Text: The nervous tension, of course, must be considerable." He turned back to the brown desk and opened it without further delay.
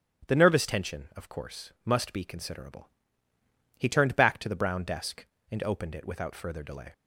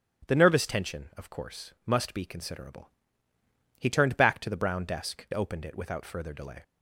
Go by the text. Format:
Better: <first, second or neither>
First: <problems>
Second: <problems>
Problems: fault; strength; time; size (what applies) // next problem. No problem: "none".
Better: first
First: starts louder than the rest; strong; until 1.3 s; 10 dB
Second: starts louder than the rest; strong; until 1.3 s; 10 dB // skips "and"; at 5.3 s